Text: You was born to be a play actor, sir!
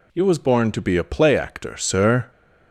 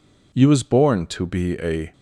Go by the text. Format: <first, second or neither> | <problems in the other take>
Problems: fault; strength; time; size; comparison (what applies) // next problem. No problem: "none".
first | stops before "play actor sir"; at 1.9 s